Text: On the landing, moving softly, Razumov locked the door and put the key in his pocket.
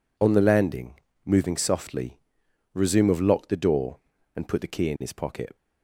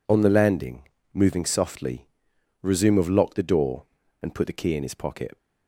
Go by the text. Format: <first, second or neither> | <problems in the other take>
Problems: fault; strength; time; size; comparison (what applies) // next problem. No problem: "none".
neither | none